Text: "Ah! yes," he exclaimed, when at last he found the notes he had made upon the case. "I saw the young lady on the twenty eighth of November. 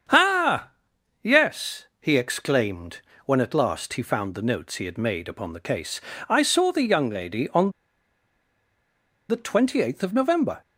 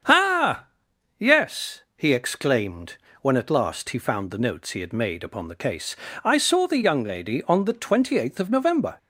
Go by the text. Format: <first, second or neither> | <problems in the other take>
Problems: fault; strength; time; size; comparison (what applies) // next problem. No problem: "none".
second | starts louder than the rest; strong; until 1.6 s; 7.5 dB; strong in the second // pauses between "on" and "the"; strong; at 7.7 s; 1.5 s long